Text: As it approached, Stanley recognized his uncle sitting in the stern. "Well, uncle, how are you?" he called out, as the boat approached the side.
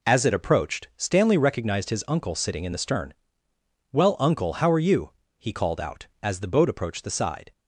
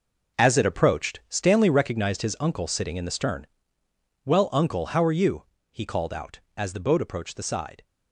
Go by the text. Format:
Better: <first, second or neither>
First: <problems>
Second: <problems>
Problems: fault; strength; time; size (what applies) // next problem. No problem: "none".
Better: first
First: none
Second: gets quieter; strong; throughout; 11 dB